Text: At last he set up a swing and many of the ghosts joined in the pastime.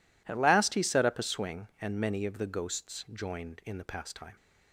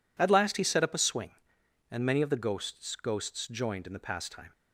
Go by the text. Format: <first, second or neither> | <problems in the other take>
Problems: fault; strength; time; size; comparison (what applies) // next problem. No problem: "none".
first | says "ghosts" twice; at 2.9 s